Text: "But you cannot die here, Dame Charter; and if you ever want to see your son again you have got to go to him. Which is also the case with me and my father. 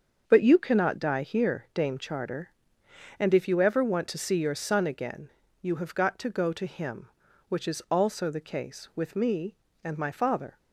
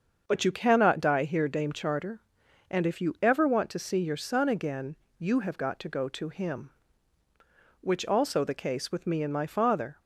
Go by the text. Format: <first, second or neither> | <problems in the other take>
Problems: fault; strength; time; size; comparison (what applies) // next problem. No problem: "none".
first | starts louder than the rest; until 1.2 s; 6.5 dB; also in the first // pauses between "again" and "you"; slight; at 4.9 s; 0.22 s long; slight in the first // skips "is"; at 8.0 s